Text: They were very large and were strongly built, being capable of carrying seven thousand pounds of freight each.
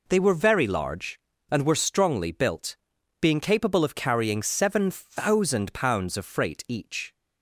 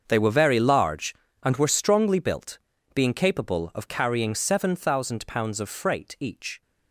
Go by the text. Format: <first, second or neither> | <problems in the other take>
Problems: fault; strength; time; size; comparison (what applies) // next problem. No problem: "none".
first | gets quieter; strong; throughout; 14.5 dB